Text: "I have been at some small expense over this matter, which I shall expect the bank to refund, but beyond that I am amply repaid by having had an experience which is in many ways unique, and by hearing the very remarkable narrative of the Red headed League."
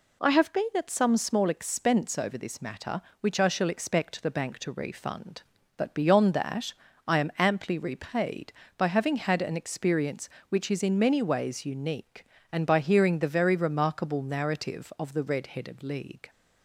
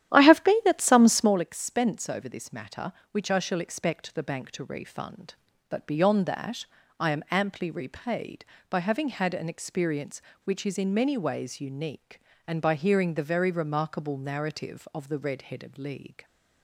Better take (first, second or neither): first